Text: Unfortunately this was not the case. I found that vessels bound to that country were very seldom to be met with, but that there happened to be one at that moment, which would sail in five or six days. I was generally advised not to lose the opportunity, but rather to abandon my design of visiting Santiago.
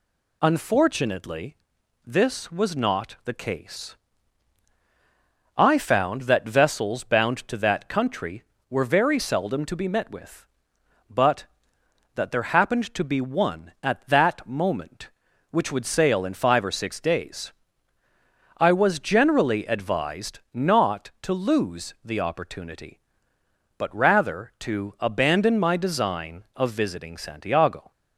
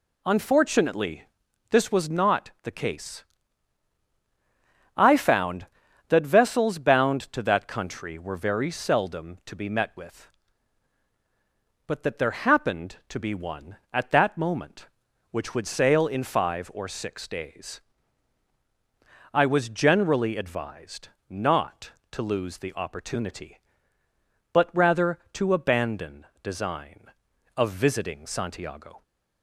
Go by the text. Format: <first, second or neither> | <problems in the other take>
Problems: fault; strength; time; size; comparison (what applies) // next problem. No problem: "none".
first | pauses between "Unfortunately" and "this"; noticeable; at 1.2 s; 0.48 s long; noticeable in the first // pauses between "advised" and "not"; slight; at 21.0 s; 0.20 s long // skips "my"; at 26.3 s